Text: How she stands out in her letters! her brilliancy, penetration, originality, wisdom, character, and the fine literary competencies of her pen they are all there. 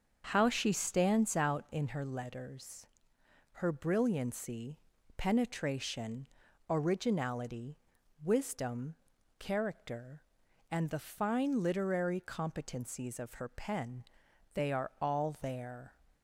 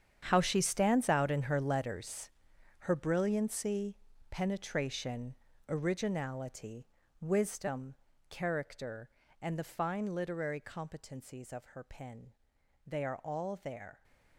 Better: first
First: starts louder than the rest; until 1.3 s; 6.5 dB // pauses between "pen" and "they"; noticeable; at 14.0 s; 0.52 s long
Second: gets quieter; strong; throughout; 14.5 dB // starts louder than the rest; strong; until 1.2 s; 8.5 dB // pauses between "pen" and "they"; noticeable; at 12.3 s; 0.56 s long

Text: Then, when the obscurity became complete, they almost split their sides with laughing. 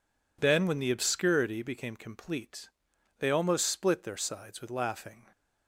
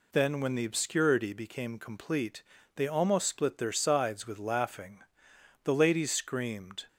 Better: first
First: none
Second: goes on to say "The ladies screamed"; noticeable; from 5.6 s on; 1.2 s long

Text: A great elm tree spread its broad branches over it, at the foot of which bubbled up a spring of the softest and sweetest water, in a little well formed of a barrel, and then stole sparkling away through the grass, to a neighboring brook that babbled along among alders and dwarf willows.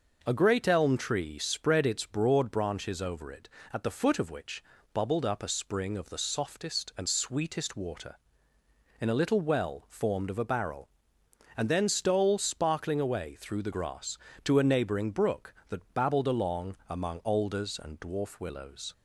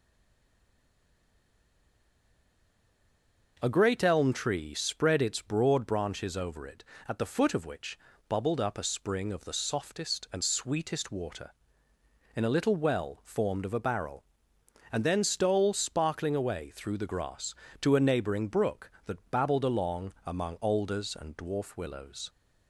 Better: first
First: pauses between "which" and "bubbled"; slight; at 4.6 s; 0.32 s long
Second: stays silent before the first word; strong; until 3.5 s; 3.5 s long // pauses between "which" and "bubbled"; slight; at 7.9 s; 0.32 s long

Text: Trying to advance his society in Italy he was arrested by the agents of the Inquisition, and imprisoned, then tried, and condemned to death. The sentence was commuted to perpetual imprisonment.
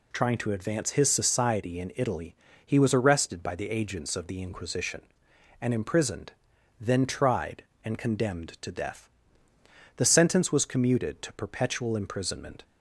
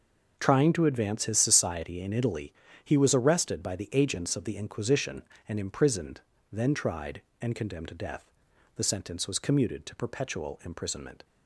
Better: neither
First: pauses between "Italy" and "he"; slight; at 2.3 s; 0.28 s long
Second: pauses between "Italy" and "he"; slight; at 2.5 s; 0.32 s long

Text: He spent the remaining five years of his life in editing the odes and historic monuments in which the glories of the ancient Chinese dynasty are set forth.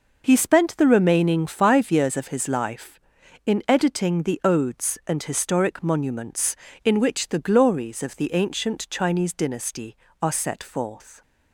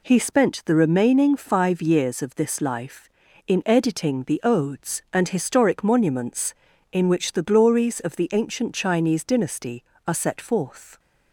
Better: first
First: none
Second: says "this" for "his"; at 2.3 s

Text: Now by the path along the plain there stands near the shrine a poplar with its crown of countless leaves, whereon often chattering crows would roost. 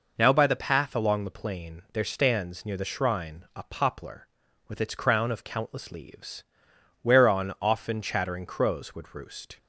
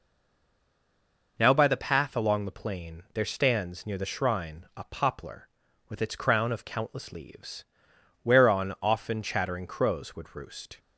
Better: first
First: none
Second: stays silent before the first word; noticeable; until 1.3 s; 1.3 s long

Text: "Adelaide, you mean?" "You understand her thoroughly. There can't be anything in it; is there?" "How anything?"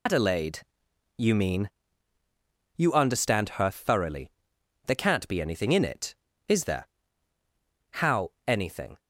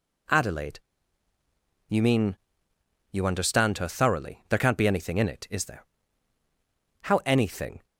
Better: second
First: loses the start of "Adelaide"; at 0.0 s; 110 ms // pauses between "How" and "anything"; slight; at 8.3 s; 0.16 s long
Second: none

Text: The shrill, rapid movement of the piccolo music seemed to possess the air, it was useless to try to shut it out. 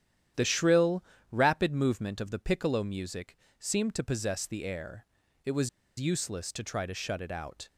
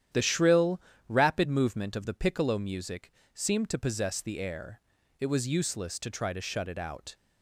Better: second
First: starts louder than the rest; strong; until 1.6 s; 10.5 dB // pauses between "music" and "seemed"; slight; at 3.3 s; 0.20 s long // pauses between "was" and "useless"; slight; at 5.6 s; 0.30 s long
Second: starts louder than the rest; strong; until 1.4 s; 10.5 dB // pauses between "music" and "seemed"; slight; at 3.1 s; 0.20 s long

